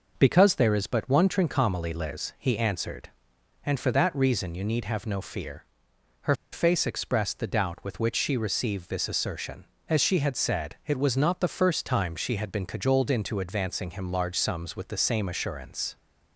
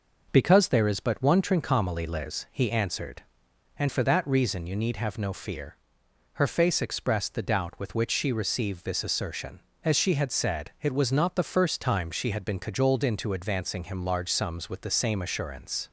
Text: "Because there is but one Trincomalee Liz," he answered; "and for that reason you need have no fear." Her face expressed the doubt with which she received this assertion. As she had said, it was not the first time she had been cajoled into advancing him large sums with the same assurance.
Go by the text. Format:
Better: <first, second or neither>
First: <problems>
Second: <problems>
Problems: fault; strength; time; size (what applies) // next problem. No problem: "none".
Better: second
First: pauses between "Her" and "face"; slight; at 6.3 s; 0.18 s long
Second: none